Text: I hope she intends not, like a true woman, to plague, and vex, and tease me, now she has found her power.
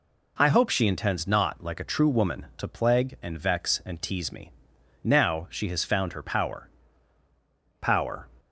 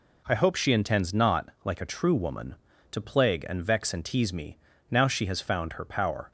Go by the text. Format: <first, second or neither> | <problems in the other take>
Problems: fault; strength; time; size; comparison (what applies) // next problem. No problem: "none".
second | says "power" twice; at 7.8 s